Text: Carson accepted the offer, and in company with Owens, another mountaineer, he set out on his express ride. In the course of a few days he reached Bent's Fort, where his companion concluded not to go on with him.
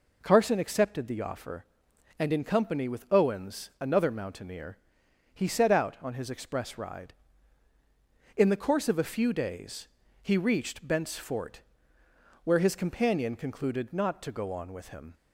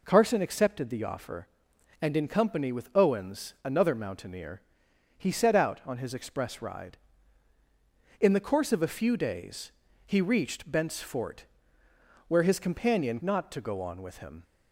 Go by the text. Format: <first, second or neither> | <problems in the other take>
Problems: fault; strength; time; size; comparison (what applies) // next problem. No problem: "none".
first | pauses between "days" and "he"; slight; at 9.7 s; 0.34 s long; slight in the first // skips "concluded"; at 13.2 s